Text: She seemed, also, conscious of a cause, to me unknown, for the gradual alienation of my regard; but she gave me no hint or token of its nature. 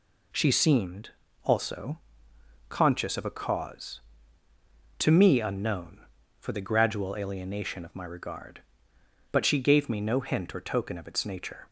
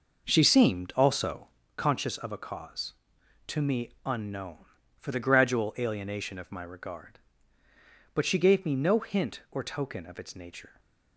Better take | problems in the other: first | starts louder than the rest; noticeable; until 1.7 s; 5.5 dB

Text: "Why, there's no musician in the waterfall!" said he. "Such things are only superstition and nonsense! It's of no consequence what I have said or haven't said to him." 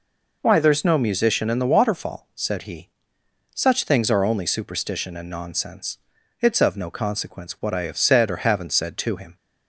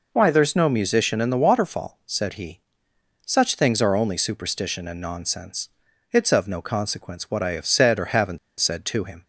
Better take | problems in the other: first | pauses between "haven't" and "said"; slight; at 8.3 s; 0.21 s long

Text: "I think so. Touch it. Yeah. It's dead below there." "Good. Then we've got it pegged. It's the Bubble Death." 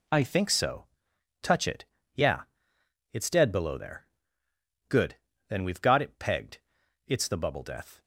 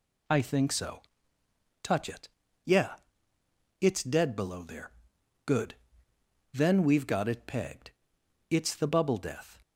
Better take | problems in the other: second | changes voice at "think"; from 0.2 s on; 7.8 s long

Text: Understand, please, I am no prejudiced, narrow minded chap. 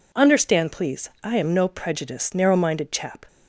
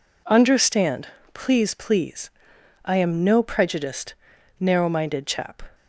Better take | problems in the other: first | says "please" twice; at 1.7 s

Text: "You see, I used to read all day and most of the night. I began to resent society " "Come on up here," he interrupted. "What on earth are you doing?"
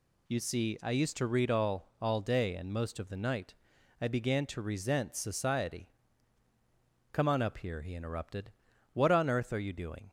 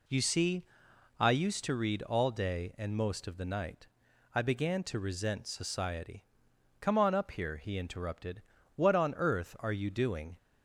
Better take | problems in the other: second | says "all" twice; at 2.0 s

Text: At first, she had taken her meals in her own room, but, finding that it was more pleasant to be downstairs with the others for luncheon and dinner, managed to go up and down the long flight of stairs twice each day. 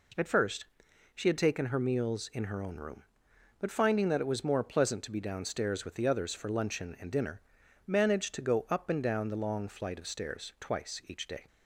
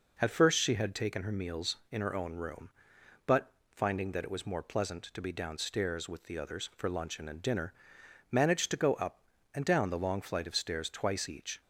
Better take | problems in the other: first | stops before "day"; at 11.6 s

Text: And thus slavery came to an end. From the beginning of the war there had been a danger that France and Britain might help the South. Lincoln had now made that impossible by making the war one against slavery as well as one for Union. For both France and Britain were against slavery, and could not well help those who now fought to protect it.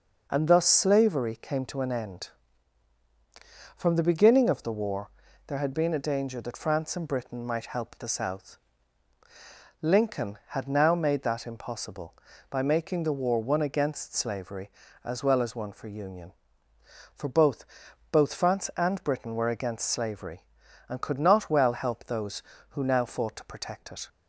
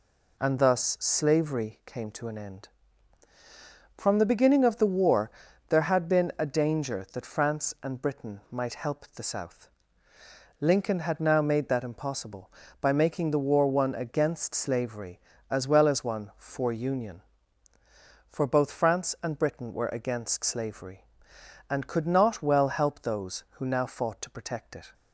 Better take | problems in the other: second | pauses between "war" and "there"; slight; at 5.0 s; 0.36 s long; also in the second // says "both" twice; at 18.1 s

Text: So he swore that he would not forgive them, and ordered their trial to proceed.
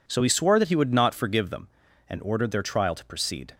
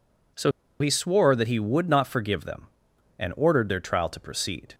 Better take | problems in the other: first | pauses between "So" and "he"; slight; at 0.5 s; 0.29 s long

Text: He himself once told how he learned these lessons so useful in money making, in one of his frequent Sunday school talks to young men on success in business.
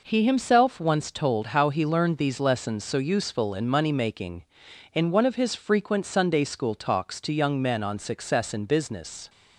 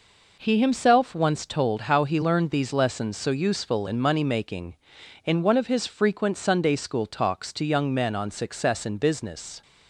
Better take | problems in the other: neither | none

